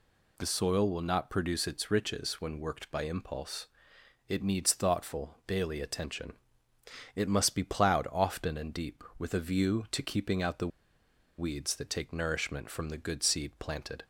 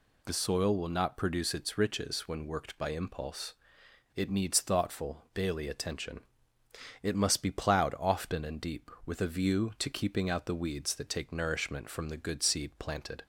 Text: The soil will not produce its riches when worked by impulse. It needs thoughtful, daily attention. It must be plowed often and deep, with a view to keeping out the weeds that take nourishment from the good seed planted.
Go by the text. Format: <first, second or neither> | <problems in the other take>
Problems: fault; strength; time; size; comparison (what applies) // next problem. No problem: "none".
second | pauses between "the" and "weeds"; noticeable; at 10.6 s; 0.70 s long